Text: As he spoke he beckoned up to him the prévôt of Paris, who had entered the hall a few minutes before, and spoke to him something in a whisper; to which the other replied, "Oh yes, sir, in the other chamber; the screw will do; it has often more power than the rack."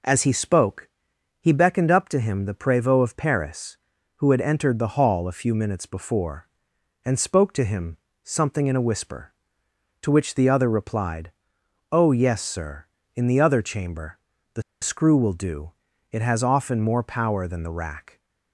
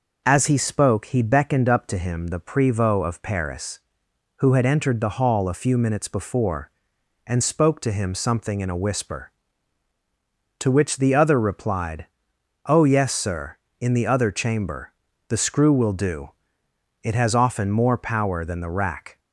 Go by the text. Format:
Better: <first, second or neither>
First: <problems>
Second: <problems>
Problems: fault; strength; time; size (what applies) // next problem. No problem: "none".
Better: second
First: pauses between "spoke" and "he"; noticeable; at 0.8 s; 0.54 s long // pauses between "him" and "something"; slight; at 7.9 s; 0.26 s long // pauses between "the" and "screw"; slight; at 14.6 s; 0.19 s long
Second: none